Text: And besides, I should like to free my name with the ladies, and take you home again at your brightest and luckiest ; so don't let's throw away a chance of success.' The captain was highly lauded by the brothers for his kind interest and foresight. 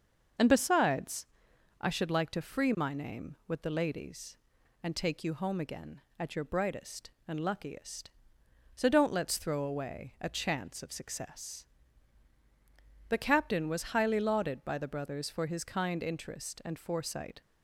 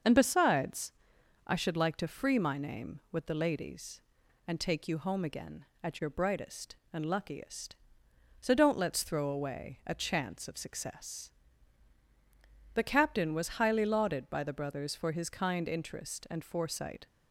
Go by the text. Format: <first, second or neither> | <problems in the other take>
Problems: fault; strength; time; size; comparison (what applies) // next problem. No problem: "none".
neither | starts louder than the rest; the same in both